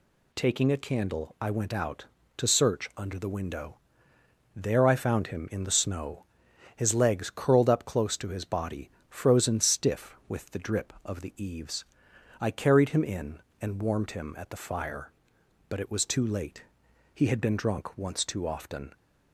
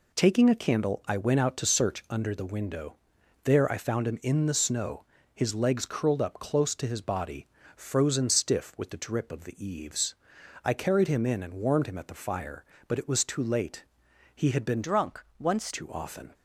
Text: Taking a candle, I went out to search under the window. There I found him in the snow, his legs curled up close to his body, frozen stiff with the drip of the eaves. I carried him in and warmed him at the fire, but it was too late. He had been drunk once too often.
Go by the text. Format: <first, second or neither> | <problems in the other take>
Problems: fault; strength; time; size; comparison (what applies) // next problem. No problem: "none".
first | changes voice from "drunk" to "once"; from 14.8 to 15.7 s; 0.9 s long // pauses between "drunk" and "once"; slight; at 15.2 s; 0.16 s long